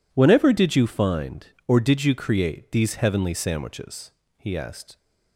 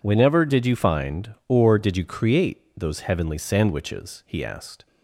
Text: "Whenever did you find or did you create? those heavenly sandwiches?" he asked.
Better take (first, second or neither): second